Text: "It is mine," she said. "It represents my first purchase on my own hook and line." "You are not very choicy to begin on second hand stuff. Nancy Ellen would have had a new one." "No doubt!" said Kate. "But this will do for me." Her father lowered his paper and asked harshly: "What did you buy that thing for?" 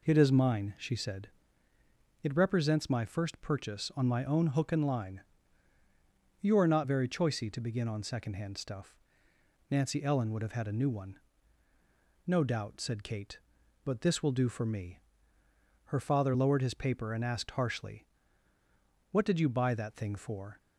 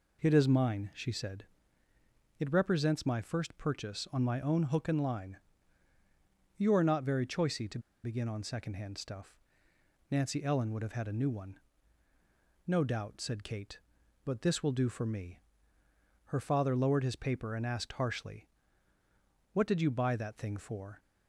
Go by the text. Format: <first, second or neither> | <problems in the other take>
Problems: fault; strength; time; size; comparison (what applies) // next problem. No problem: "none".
first | pauses between "to" and "begin"; slight; at 7.7 s; 0.24 s long